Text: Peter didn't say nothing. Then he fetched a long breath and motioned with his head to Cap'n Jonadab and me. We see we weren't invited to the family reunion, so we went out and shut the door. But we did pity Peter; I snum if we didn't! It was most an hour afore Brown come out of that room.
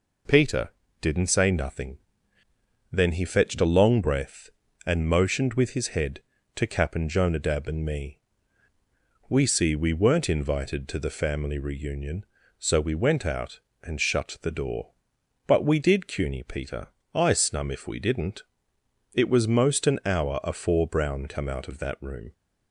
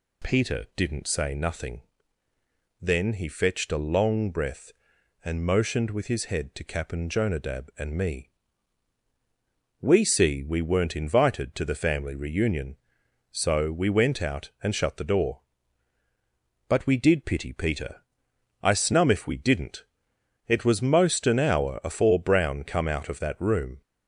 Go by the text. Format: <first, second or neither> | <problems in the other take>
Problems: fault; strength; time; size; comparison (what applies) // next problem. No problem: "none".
second | pauses between "Peter" and "didn't"; slight; at 0.7 s; 0.30 s long // says "cuny" for "pity"; at 16.0 s